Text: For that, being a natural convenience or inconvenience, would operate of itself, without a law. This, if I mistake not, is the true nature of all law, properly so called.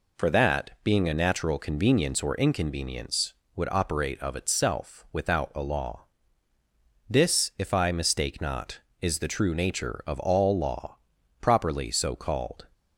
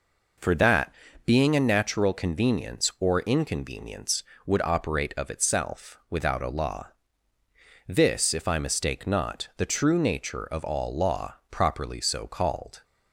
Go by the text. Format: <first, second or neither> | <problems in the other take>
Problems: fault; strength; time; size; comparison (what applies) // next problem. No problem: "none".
first | skips "is"; at 9.5 s